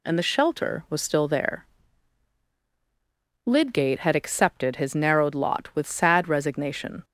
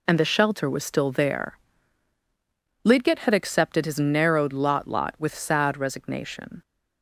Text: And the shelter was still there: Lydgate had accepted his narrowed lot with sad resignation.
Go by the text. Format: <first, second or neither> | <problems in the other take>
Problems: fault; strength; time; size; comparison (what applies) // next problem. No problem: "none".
first | says "lot" twice; at 4.8 s